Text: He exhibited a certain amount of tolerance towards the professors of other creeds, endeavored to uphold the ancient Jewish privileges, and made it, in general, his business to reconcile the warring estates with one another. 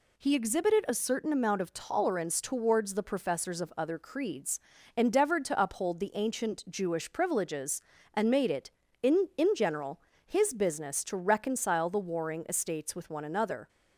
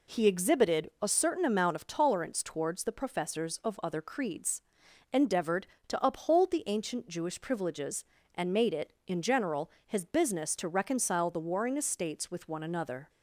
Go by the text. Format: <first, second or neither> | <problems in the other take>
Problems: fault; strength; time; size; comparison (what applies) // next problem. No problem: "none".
second | says "in" twice; at 9.3 s